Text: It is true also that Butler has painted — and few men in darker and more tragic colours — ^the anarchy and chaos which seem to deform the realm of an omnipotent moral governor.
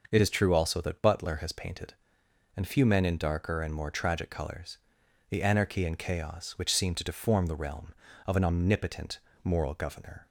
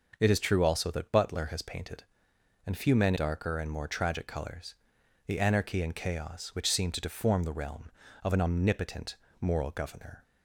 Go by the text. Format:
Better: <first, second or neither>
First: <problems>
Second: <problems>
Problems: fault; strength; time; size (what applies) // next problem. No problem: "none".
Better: first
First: starts louder than the rest; noticeable; until 1.1 s; 6 dB // pauses between "omnipotent" and "moral"; slight; at 9.1 s; 0.24 s long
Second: starts louder than the rest; noticeable; until 1.2 s; 6 dB // skips "in"; at 3.1 s // pauses between "omnipotent" and "moral"; slight; at 9.1 s; 0.24 s long